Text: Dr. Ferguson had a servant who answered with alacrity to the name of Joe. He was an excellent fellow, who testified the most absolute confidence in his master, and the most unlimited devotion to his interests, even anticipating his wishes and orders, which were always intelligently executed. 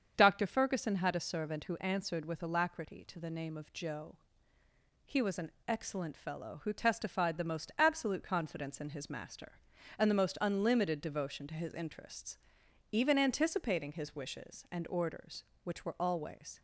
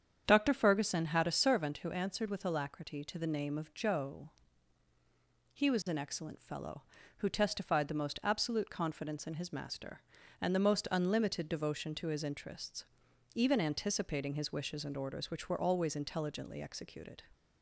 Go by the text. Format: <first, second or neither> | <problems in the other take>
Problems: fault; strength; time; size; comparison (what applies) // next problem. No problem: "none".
second | starts louder than the rest; strong; until 1.1 s; 7 dB; strong in the second // pauses between "an" and "excellent"; slight; at 5.5 s; 0.16 s long // stops before "intelligently executed"; at 16.5 s